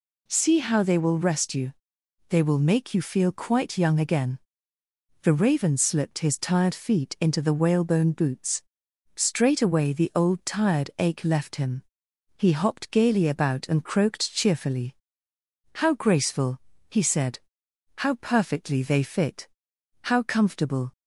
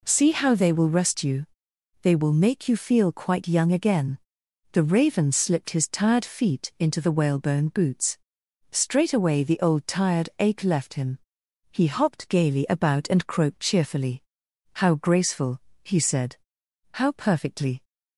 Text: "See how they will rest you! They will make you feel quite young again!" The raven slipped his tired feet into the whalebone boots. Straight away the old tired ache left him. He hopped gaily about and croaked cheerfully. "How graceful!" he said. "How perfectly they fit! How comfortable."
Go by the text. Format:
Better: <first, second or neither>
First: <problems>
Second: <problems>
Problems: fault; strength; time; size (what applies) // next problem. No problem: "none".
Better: first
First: none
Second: stops before "they fit How comfortable"; at 17.8 s